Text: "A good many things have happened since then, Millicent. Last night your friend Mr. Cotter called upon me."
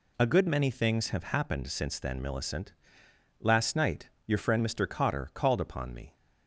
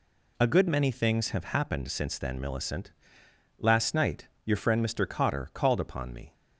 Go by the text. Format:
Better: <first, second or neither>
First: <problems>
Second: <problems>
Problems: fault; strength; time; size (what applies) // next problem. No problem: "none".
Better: neither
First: pauses between "night" and "your"; slight; at 4.0 s; 0.18 s long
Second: pauses between "night" and "your"; slight; at 4.2 s; 0.18 s long